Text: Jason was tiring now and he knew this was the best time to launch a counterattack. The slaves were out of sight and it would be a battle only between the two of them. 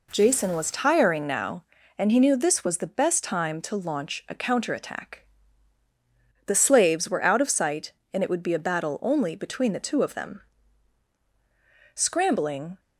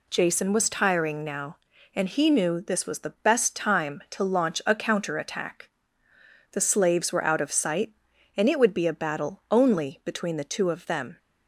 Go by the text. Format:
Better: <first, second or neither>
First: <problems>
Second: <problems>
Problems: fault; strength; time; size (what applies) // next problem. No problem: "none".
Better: second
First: goes on to say "Scrambling"; noticeable; from 11.9 s on; 0.84 s long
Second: none